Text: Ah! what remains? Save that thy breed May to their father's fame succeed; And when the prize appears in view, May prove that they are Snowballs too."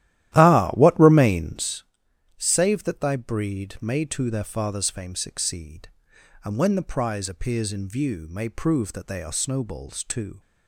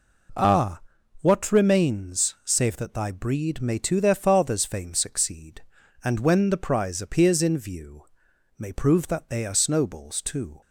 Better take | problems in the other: second | starts louder than the rest; strong; until 1.8 s; 13.5 dB

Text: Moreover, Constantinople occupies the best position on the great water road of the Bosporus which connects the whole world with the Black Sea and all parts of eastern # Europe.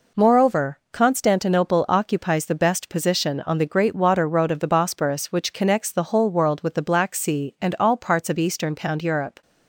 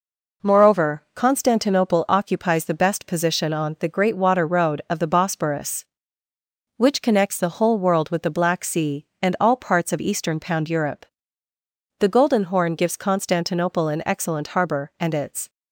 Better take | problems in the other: first | goes on to say "The Golden Horn gives Constantinople an excellent harbor and its"; strong; from 11.9 s on; 3.5 s long

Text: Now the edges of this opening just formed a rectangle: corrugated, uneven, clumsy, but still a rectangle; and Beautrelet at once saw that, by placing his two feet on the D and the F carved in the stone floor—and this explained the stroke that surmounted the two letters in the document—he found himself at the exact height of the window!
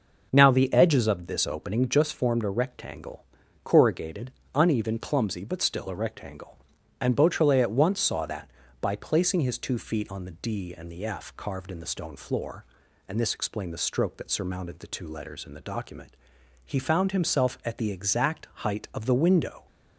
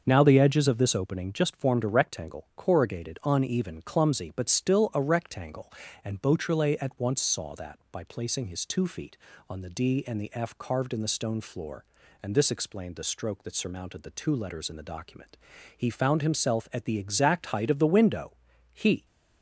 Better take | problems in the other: first | starts louder than the rest; until 1.0 s; 6.5 dB // goes on to say "He"; slight; from 18.7 s on; 0.32 s long

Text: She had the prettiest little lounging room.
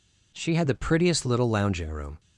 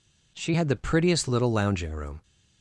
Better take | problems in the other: neither | none

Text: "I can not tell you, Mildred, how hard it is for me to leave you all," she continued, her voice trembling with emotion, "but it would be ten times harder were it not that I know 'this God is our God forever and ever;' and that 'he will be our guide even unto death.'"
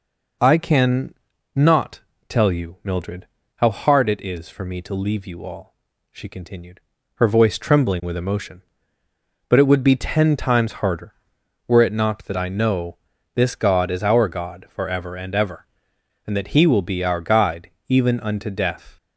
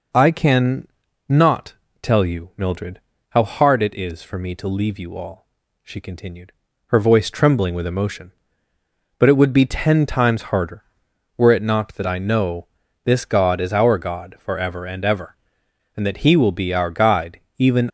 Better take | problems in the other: first | pauses between "can" and "not"; at 0.8 s; 0.40 s long; also in the first // pauses between "not" and "tell"; slight; at 1.7 s; 0.28 s long; slight in the first // pauses between "know" and "this"; at 12.6 s; 0.38 s long; also in the first // pauses between "guide" and "even"; slight; at 17.3 s; 0.18 s long; slight in the first // stops before "unto death"; at 17.8 s

